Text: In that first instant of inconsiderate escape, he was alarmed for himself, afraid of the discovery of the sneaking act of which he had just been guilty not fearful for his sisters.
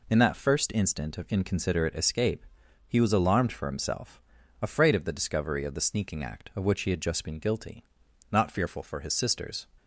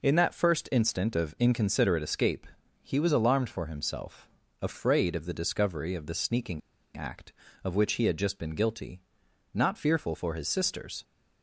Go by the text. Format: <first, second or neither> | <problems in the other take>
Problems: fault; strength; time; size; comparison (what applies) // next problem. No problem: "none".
first | pauses between "sneaking" and "act"; at 6.6 s; 0.36 s long // pauses between "guilty" and "not"; noticeable; at 9.0 s; 0.52 s long; noticeable in the first